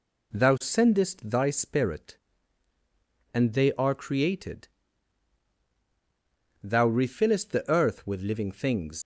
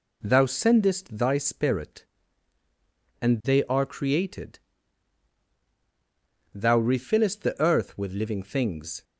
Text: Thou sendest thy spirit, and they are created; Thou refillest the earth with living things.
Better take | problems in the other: second | leaves "things" unfinished; at 9.0 s; 105 ms

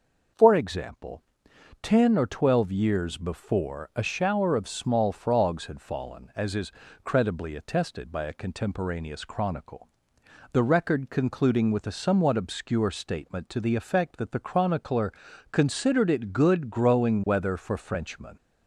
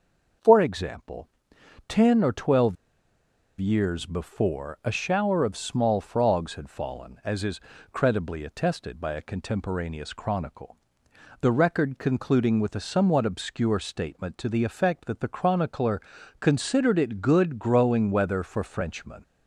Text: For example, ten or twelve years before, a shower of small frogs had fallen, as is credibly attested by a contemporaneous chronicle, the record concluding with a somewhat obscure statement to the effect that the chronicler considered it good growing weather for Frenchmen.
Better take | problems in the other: first | starts louder than the rest; until 2.0 s; 6 dB; also in the first // pauses between "twelve" and "years"; noticeable; at 2.7 s; 0.84 s long // pauses between "is" and "credibly"; slight; at 7.6 s; 0.32 s long; slight in the first // pauses between "chronicler" and "considered"; at 16.0 s; 0.40 s long; also in the first

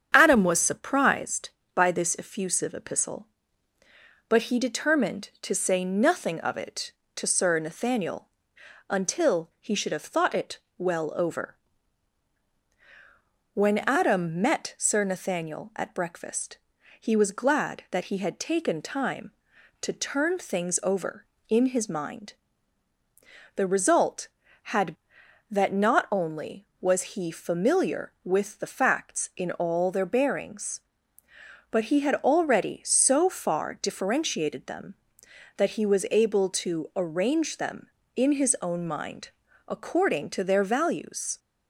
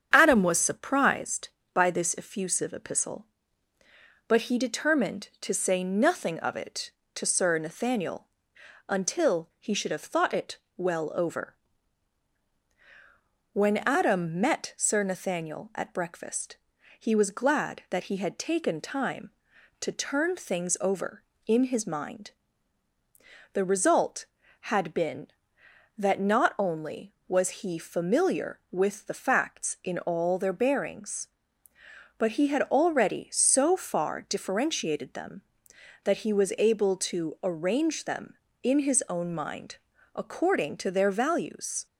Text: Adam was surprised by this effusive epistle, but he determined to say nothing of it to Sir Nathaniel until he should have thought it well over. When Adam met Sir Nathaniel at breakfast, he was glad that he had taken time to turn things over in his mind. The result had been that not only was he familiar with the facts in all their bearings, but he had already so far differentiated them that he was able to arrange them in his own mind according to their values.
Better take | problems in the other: second | starts louder than the rest; strong; until 1.1 s; 8 dB; strong in the second // pauses between "Nathaniel" and "until"; noticeable; at 8.2 s; 0.62 s long; noticeable in the second // pauses between "it" and "well"; slight; at 10.5 s; 0.18 s long; slight in the second // skips "been"; at 25.2 s // pauses between "mind" and "according"; at 39.3 s; 0.38 s long; also in the second

